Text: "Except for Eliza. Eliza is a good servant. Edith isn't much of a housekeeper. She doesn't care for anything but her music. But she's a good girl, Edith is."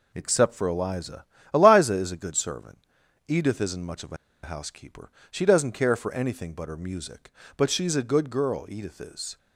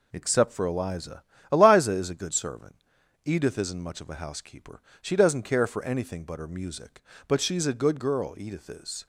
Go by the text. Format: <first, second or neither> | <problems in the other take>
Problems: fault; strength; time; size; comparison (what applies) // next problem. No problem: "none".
second | pauses between "a" and "housekeeper"; slight; at 4.1 s; 0.28 s long